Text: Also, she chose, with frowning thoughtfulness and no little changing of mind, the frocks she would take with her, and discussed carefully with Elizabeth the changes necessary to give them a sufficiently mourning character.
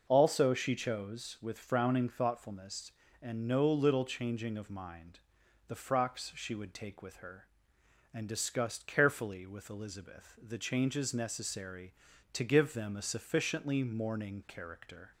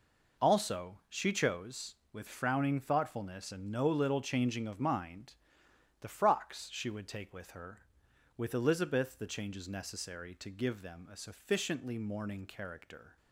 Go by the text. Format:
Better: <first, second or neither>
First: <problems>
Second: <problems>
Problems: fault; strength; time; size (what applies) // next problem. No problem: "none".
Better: first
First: none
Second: skips "and discussed carefully"; at 8.0 s